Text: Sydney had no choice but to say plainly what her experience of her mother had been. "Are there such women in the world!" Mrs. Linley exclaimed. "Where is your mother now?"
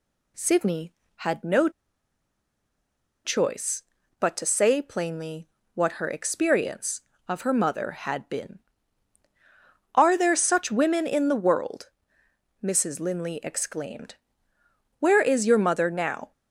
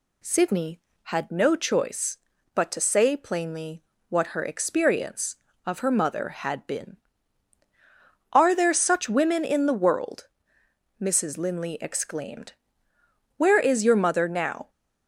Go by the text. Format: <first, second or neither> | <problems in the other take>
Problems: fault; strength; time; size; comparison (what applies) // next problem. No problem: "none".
second | pauses between "no" and "choice"; strong; at 1.6 s; 1.5 s long // pauses between "plainly" and "what"; slight; at 5.4 s; 0.26 s long; slight in the second